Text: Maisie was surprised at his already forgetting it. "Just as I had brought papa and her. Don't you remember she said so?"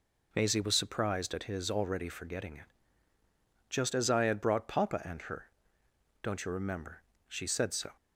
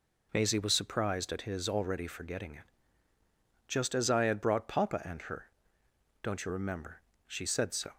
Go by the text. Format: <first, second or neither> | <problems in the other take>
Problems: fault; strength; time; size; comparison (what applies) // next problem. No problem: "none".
neither | pauses between "remember" and "she"; slight; the same in both